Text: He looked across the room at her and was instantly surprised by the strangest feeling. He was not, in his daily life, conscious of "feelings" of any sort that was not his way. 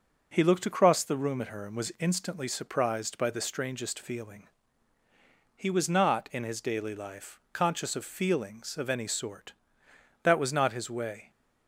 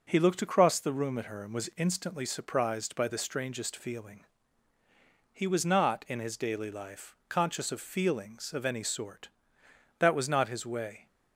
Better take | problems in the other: neither | none

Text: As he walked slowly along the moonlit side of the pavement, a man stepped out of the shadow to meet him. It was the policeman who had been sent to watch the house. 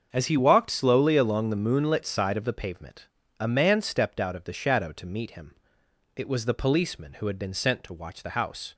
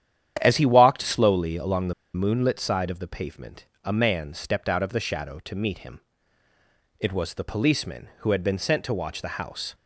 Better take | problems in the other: first | starts louder than the rest; strong; until 1.4 s; 10 dB; also in the first // pauses between "the" and "moonlit"; slight; at 1.9 s; 0.20 s long

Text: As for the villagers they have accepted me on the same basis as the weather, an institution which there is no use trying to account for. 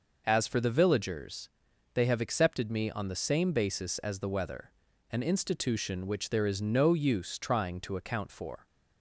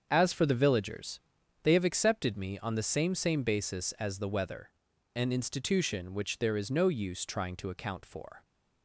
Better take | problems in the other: first | starts louder than the rest; strong; until 1.1 s; 7 dB // pauses between "villagers" and "they"; at 1.2 s; 0.42 s long; noticeable in the first // says "same" twice; at 3.1 s

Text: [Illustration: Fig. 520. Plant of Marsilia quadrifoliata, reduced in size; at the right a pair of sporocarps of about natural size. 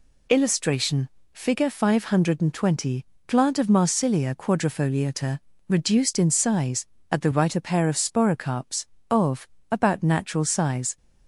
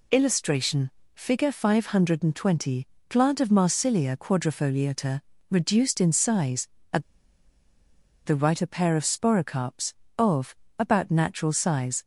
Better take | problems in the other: first | pauses between "at" and "the"; at 7.0 s; 1.2 s long // pauses between "of" and "about"; slight; at 10.5 s; 0.24 s long; slight in the first

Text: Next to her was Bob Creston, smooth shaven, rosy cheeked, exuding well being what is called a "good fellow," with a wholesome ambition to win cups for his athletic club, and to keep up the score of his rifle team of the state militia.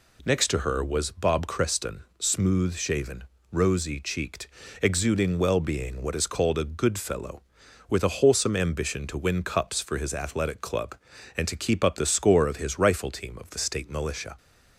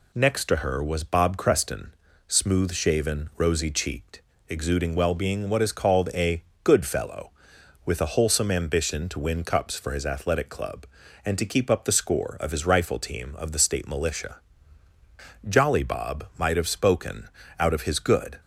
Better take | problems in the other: first | pauses between "a" and "good"; slight; at 6.4 s; 0.22 s long // goes on to say "Jolly Bob might have spoken out of his good"; strong; from 15.4 s on; 2.9 s long

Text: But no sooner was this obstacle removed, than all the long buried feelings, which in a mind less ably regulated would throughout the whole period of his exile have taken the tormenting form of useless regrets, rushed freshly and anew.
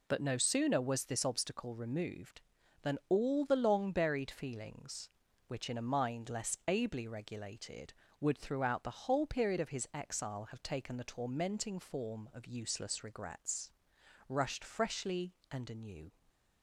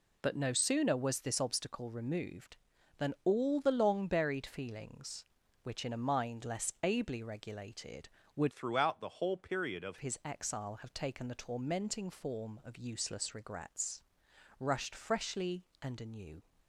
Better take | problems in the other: first | changes voice from "throughout" to "of"; from 8.5 to 9.9 s; 1.4 s long

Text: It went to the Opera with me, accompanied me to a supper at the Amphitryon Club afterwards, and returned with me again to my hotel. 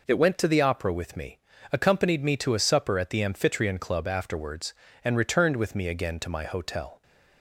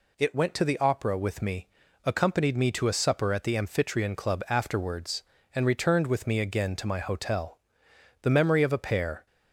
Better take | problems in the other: first | goes on to say "The memory of a pair"; noticeable; from 8.2 s on; 1.0 s long

